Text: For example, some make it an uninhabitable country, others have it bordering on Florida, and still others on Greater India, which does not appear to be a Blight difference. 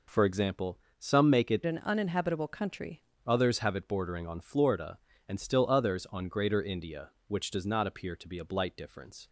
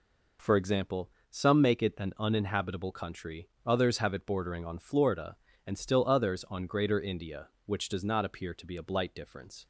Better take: second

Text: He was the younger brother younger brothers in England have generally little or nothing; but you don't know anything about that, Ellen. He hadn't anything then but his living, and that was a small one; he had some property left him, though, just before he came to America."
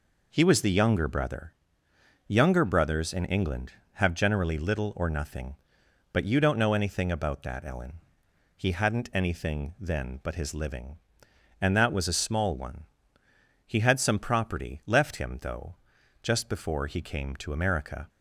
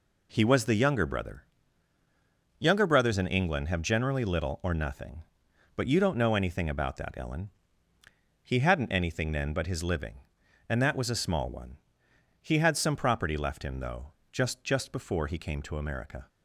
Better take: first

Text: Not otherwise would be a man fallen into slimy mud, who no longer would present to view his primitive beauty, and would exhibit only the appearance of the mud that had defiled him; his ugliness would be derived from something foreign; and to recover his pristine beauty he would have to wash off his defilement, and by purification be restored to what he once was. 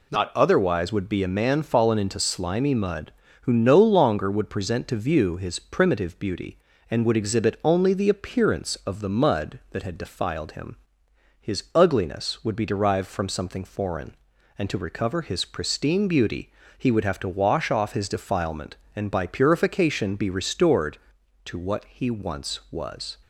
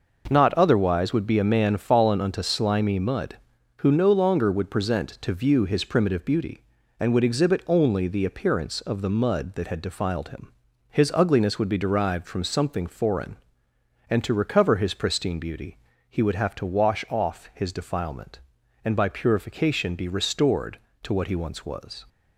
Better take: first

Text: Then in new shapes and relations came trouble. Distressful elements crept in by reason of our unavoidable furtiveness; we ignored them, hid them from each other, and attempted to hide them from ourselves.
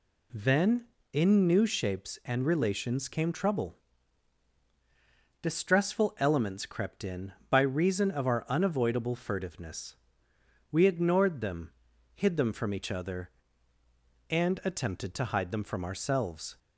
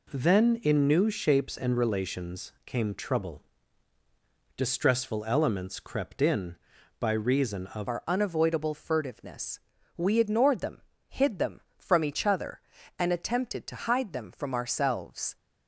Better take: first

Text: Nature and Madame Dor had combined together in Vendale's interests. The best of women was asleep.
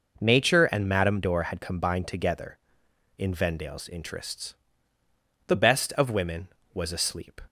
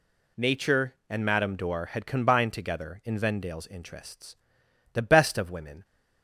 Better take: first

